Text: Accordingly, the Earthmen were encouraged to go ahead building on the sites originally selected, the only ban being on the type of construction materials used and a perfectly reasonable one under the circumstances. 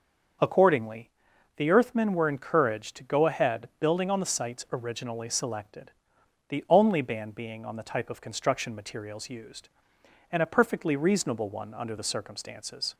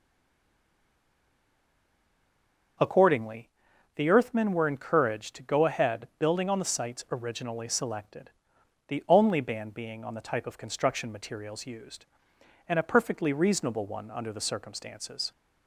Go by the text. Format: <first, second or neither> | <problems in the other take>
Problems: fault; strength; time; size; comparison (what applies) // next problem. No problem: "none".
first | stays silent before the first word; strong; until 2.7 s; 2.7 s long // starts louder than the rest; until 4.2 s; 6.5 dB; also in the first